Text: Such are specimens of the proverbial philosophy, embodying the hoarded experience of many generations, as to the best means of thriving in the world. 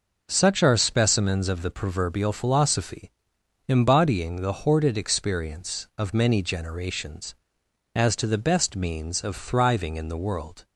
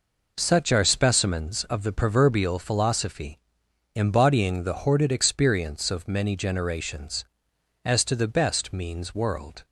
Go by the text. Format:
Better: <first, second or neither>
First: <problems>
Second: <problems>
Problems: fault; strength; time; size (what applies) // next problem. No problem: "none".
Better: first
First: none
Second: skips "of thriving in the"; at 9.1 s